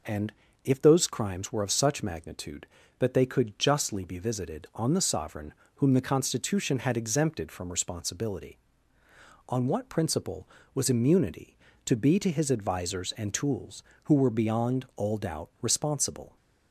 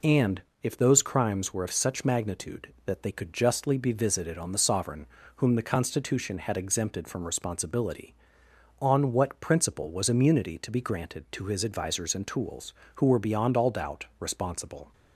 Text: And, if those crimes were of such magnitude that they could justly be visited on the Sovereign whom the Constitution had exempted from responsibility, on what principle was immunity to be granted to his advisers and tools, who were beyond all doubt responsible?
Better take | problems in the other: second | pauses between "Sovereign" and "whom"; slight; at 5.5 s; 0.22 s long; slight in the second // skips "granted"; at 12.1 s

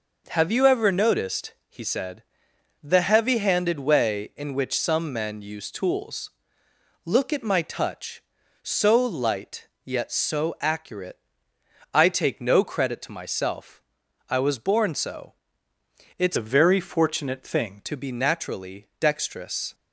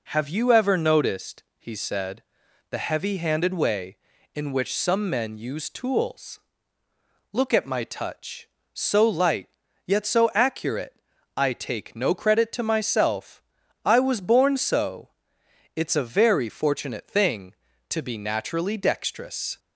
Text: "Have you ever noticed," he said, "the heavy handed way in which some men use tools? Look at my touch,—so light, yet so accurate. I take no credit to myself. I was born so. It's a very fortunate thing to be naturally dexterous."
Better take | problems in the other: second | changes voice from "a" to "thing"; from 16.3 to 17.7 s; 1.4 s long

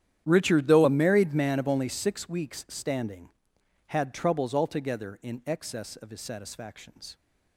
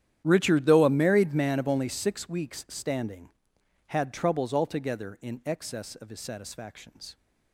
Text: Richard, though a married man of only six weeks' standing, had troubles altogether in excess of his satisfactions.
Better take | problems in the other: neither | starts louder than the rest; strong; the same in both

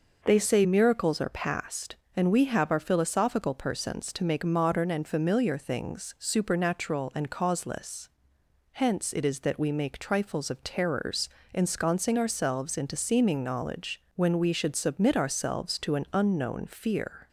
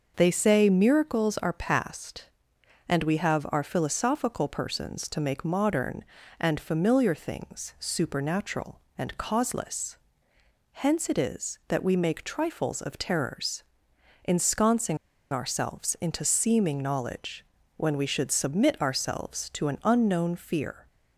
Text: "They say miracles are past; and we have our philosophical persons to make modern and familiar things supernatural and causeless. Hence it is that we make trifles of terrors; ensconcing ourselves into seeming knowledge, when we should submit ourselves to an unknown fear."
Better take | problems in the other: first | pauses between "ensconcing" and "ourselves"; slight; at 14.9 s; 0.35 s long

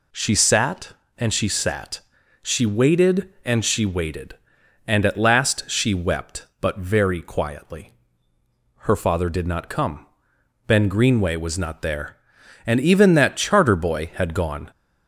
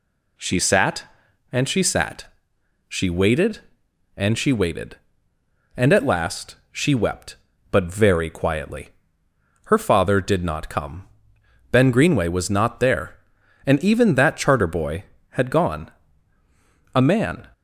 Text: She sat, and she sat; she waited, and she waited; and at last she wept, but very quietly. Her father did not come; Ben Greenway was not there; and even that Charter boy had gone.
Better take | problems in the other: first | goes on to say "A man"; from 16.9 s on; 0.54 s long

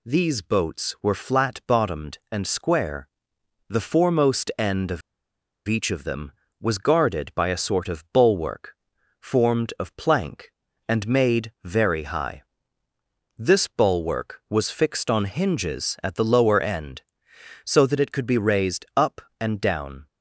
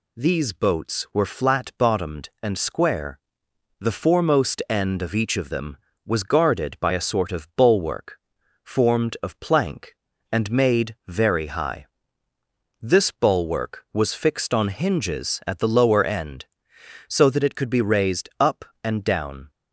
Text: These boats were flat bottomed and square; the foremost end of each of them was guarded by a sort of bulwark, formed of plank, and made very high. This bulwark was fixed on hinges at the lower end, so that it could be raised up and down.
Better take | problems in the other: second | pauses between "of" and "each"; noticeable; at 5.0 s; 0.67 s long

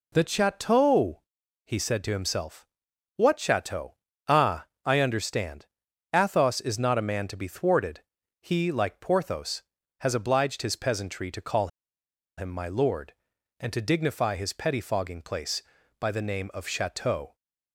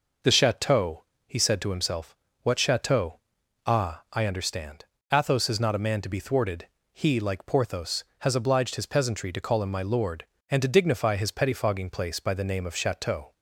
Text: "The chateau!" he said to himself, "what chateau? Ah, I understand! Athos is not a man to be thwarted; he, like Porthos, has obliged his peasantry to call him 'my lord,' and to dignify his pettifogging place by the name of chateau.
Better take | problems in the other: second | pauses between "call" and "him"; noticeable; at 11.6 s; 0.70 s long

